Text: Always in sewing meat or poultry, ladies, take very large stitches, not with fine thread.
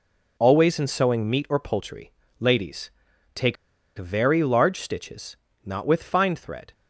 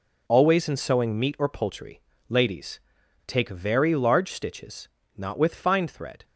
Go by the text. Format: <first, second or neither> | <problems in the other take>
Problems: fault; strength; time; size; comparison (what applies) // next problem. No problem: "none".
second | pauses between "take" and "very"; at 3.5 s; 0.42 s long